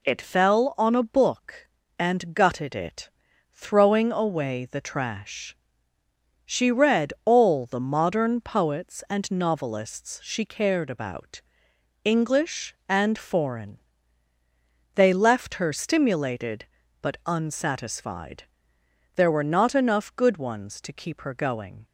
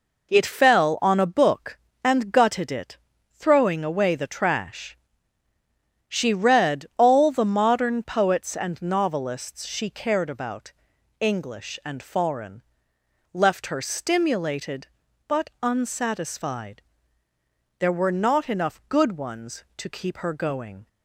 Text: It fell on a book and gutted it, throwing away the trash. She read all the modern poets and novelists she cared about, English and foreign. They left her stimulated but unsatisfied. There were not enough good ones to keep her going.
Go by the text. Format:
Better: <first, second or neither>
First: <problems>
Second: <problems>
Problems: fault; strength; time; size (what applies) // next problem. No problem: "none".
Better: first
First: none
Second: skips "They"; at 12.9 s